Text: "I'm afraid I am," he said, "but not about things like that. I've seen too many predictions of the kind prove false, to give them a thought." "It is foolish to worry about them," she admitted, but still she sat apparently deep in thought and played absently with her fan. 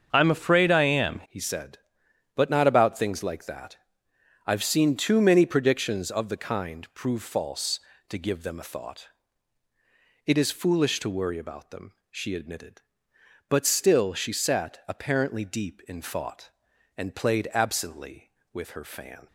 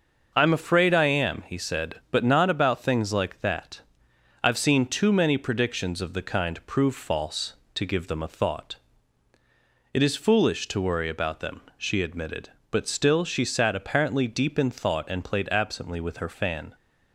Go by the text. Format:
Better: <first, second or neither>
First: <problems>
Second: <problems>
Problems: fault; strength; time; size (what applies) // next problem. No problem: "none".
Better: second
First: starts louder than the rest; until 1.1 s; 6.5 dB // changes voice at "he"; from 1.2 s on; 18.0 s long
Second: starts louder than the rest; noticeable; until 1.3 s; 6 dB